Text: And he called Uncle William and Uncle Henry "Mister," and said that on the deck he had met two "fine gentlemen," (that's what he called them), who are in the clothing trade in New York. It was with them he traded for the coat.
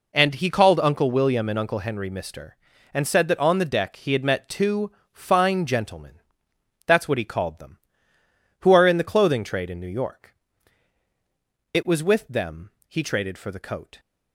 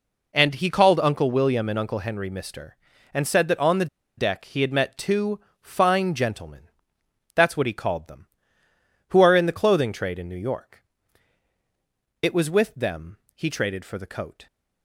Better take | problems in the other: first | pauses between "the" and "deck"; slight; at 3.8 s; 0.31 s long // pauses between "two" and "fine"; slight; at 5.3 s; 0.22 s long; slight in the first // pauses between "them" and "he"; slight; at 13.1 s; 0.16 s long; slight in the first

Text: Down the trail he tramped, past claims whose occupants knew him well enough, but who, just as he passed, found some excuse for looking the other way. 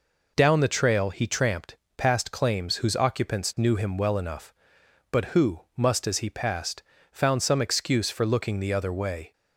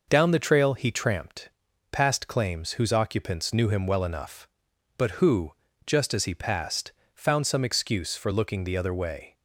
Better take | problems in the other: second | says "must" for "just"; at 5.7 s

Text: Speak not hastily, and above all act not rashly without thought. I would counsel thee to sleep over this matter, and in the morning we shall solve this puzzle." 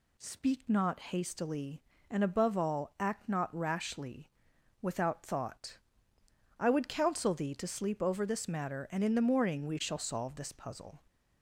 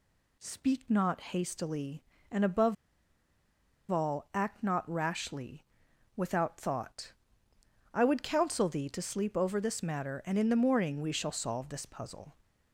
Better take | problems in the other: first | pauses between "above" and "all"; at 2.7 s; 1.1 s long // pauses between "rashly" and "without"; noticeable; at 5.6 s; 0.52 s long; noticeable in the first

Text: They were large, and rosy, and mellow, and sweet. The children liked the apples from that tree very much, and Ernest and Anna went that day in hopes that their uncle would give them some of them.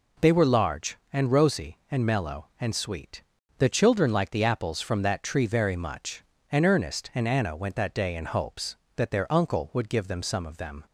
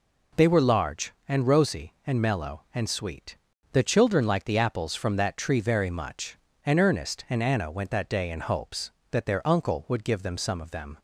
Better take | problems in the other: neither | none

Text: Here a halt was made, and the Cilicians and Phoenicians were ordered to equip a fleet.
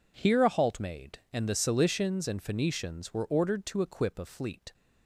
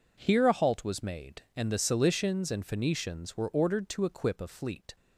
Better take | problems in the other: second | skips "was"; at 0.7 s

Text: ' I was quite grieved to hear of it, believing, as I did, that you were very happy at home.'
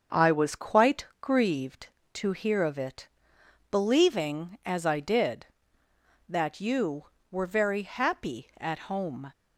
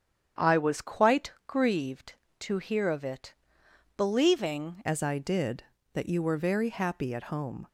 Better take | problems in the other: first | starts louder than the rest; strong; until 1.5 s; 8.5 dB; also in the first // pauses between "quite" and "grieved"; slight; at 1.3 s; 0.16 s long; slight in the first // changes voice at "as"; from 4.8 s on; 2.8 s long

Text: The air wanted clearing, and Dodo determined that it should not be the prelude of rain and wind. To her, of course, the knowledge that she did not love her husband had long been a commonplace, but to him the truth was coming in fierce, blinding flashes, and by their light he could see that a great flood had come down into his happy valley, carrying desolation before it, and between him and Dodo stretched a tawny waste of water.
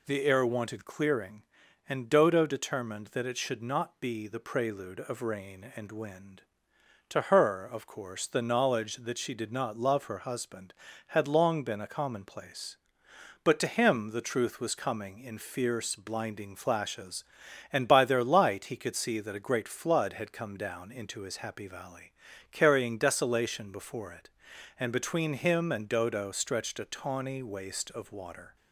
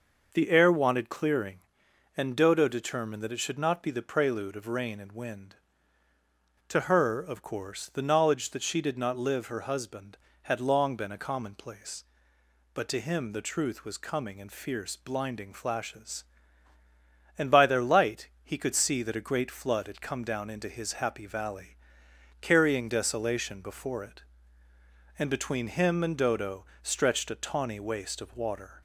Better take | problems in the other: first | says "live" for "love"; at 9.1 s // pauses between "light" and "he"; slight; at 18.2 s; 0.16 s long // pauses between "Dodo" and "stretched"; slight; at 26.6 s; 0.18 s long

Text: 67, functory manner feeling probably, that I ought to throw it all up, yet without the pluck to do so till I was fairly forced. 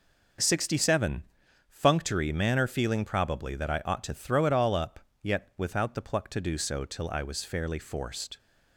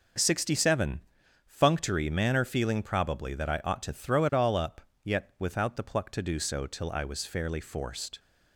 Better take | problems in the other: neither | starts louder than the rest; the same in both

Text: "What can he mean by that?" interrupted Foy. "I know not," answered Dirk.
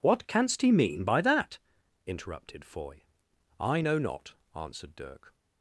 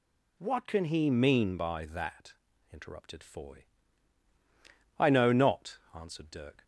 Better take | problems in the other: second | says "canst" for "can"; at 0.2 s

